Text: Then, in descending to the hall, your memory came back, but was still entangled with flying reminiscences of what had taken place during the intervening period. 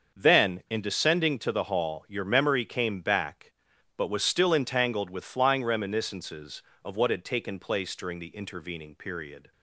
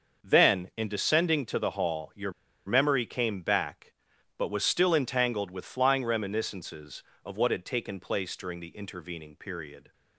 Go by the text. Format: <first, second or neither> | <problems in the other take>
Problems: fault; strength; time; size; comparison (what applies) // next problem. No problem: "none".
first | starts louder than the rest; until 1.3 s; 6.5 dB; also in the first // pauses between "your" and "memory"; slight; at 2.3 s; 0.35 s long